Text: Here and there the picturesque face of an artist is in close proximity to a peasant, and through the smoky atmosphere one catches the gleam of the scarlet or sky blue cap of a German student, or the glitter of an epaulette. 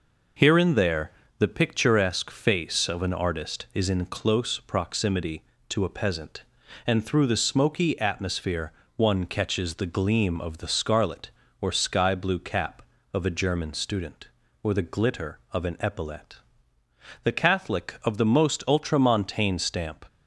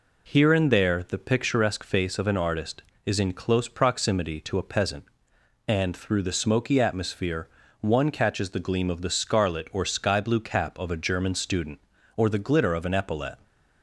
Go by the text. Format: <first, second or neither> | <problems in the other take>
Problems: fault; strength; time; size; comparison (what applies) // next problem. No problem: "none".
second | pauses between "there" and "the"; slight; at 1.0 s; 0.30 s long // pauses between "atmosphere" and "one"; slight; at 8.7 s; 0.26 s long; slight in the second // goes on to say "The Catholic of the most ultramontane stamp"; strong; from 17.2 s on; 2.8 s long